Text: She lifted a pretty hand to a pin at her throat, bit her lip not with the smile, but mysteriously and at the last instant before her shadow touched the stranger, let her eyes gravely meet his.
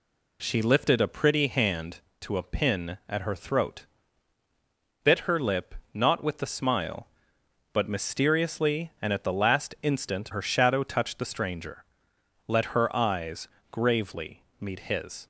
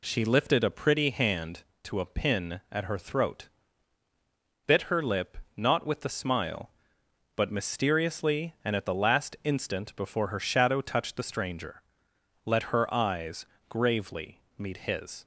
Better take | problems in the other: second | pauses between "lip" and "not"; slight; at 5.7 s; 0.18 s long; slight in the second // skips "before"; at 10.3 s // pauses between "eyes" and "gravely"; slight; at 13.4 s; 0.24 s long; slight in the second // pauses between "gravely" and "meet"; slight; at 14.4 s; 0.18 s long; slight in the second

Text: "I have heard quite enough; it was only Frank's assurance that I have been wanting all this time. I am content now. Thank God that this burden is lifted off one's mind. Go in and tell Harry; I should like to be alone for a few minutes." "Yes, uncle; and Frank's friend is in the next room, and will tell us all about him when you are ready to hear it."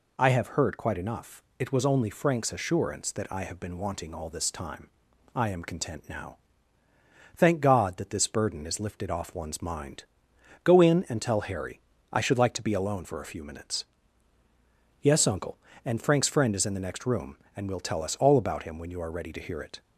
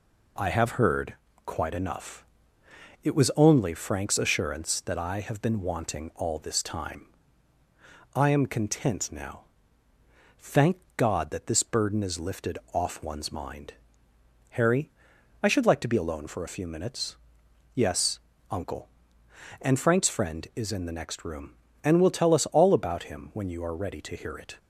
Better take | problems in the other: first | pauses between "heard" and "quite"; slight; at 1.1 s; 0.32 s long // pauses between "Thank" and "God"; slight; at 10.7 s; 0.22 s long // pauses between "lifted" and "off"; slight; at 12.5 s; 0.16 s long // skips "Go in and tell"; at 14.1 s

